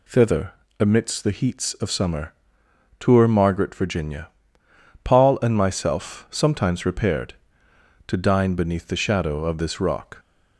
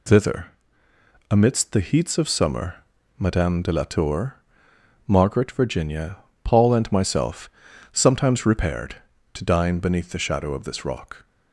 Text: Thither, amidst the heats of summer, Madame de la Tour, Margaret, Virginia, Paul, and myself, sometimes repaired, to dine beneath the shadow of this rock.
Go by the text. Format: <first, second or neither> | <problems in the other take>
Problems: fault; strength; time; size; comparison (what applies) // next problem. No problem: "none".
second | skips "Madame de la"; at 2.6 s